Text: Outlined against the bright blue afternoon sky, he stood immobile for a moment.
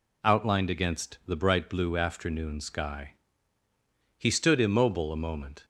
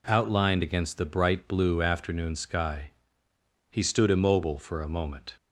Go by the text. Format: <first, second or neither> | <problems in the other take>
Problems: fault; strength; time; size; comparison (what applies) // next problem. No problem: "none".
second | skips "for"; at 5.1 s